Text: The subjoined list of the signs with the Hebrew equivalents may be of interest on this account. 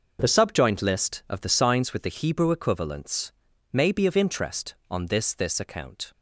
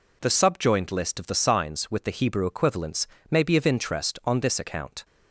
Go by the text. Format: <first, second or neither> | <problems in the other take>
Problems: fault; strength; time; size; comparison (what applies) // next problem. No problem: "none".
second | pauses between "equivalents" and "may"; at 3.3 s; 0.40 s long; slight in the second // says "this" twice; at 5.3 s